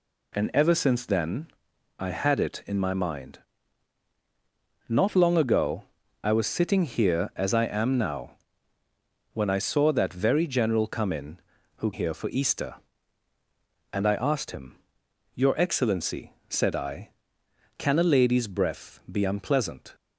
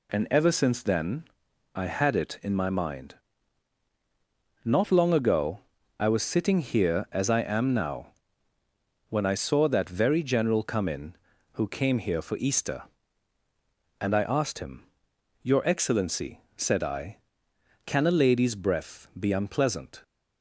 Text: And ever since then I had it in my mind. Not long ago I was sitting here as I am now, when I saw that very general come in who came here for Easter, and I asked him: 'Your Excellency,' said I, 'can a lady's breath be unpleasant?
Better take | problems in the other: second | pauses between "then" and "I"; noticeable; at 1.4 s; 0.52 s long; noticeable in the second // pauses between "ago" and "I"; at 5.8 s; 0.40 s long; also in the second // skips "came"; at 11.9 s

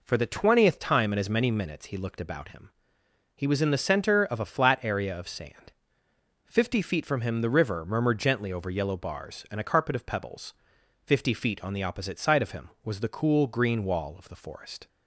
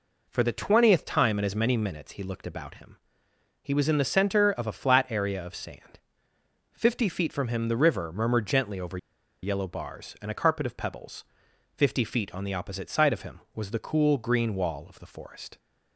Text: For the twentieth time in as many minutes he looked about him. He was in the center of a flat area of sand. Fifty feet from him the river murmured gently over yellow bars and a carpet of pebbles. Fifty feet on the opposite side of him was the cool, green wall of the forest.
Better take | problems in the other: first | pauses between "over" and "yellow"; at 8.9 s; 0.45 s long

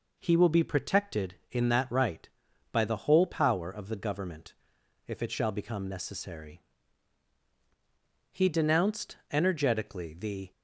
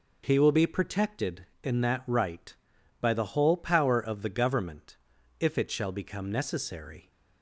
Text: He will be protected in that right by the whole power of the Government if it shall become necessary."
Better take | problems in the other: second | pauses between "Government" and "if"; noticeable; at 4.5 s; 0.54 s long; also in the second // goes on to say "He denounced energetically the"; strong; from 8.3 s on; 2.1 s long

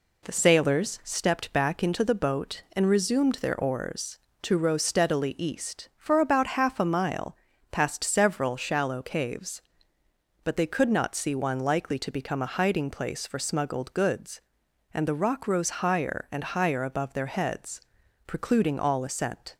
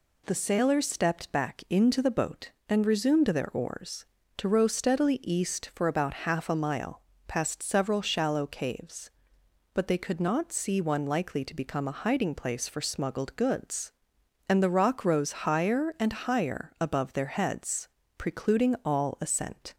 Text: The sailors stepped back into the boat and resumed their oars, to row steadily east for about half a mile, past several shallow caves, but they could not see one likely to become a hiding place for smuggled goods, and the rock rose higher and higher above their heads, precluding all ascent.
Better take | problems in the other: neither | none

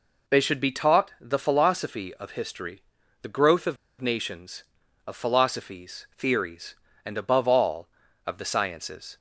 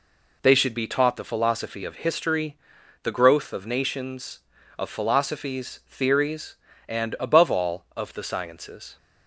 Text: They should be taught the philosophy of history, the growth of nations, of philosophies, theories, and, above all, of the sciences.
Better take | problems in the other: second | pauses between "of" and "nations"; slight; at 3.7 s; 0.24 s long

